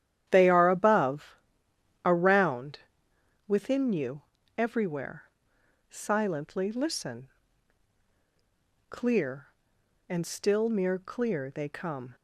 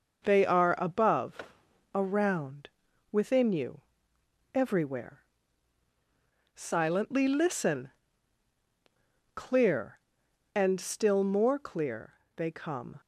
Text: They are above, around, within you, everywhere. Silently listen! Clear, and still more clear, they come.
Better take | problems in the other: second | starts louder than the rest; strong; until 1.2 s; 11 dB // says "mere" for "more"; at 10.6 s

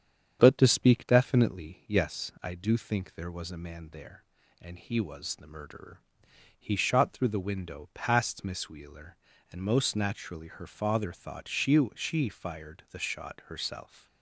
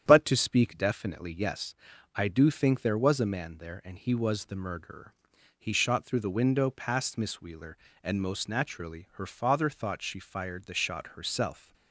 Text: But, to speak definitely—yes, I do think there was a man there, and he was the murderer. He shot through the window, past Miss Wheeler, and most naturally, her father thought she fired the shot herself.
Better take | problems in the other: second | starts louder than the rest; strong; until 1.4 s; 8 dB; strong in the second // says "she" twice; at 11.9 s

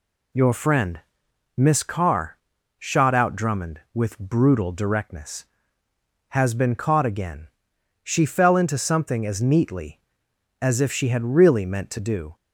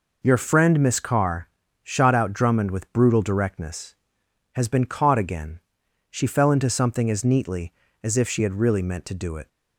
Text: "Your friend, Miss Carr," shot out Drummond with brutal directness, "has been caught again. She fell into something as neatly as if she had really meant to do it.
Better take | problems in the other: second | stops before "it"; at 12.3 s

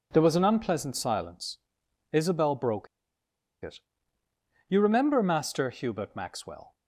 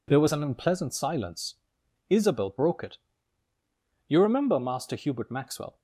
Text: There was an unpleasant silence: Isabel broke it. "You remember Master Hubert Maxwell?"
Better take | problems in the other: second | pauses between "broke" and "it"; noticeable; at 2.8 s; 0.77 s long

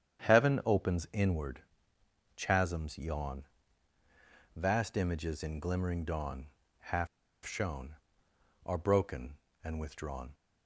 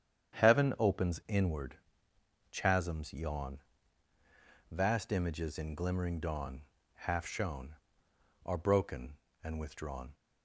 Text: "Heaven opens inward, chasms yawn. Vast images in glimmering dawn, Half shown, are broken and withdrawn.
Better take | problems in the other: second | starts louder than the rest; strong; until 1.3 s; 9 dB; strong in the second // pauses between "Half" and "shown"; at 7.0 s; 0.38 s long

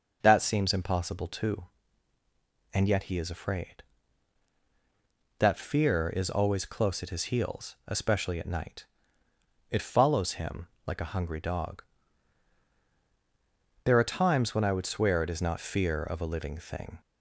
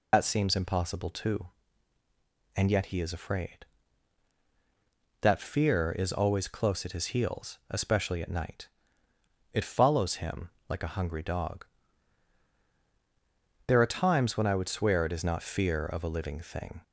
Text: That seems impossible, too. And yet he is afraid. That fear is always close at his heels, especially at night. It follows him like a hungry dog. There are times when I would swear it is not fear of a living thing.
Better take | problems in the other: first | loses the start of "That"; at 0.1 s; 85 ms // pauses between "him" and "like"; slight; at 10.4 s; 0.20 s long; slight in the first

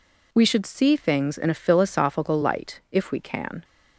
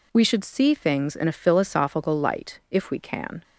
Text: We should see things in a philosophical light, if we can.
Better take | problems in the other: neither | none

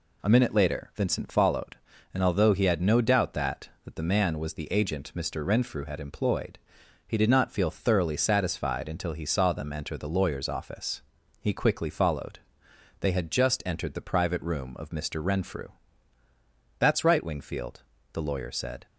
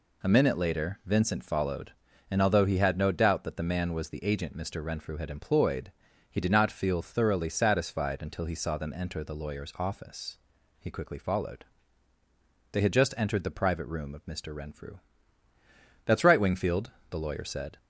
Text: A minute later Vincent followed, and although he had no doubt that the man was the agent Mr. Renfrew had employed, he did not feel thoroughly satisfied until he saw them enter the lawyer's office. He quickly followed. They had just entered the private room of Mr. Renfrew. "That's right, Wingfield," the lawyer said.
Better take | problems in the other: second | says "that" twice; at 3.8 s

